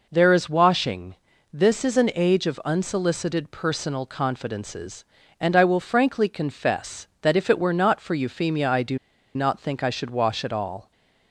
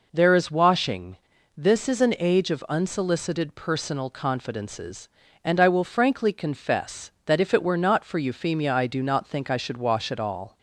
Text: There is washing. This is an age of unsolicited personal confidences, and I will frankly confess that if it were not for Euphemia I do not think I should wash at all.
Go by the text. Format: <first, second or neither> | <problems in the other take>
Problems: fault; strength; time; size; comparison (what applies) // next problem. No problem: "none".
second | pauses between "do" and "not"; at 8.9 s; 0.37 s long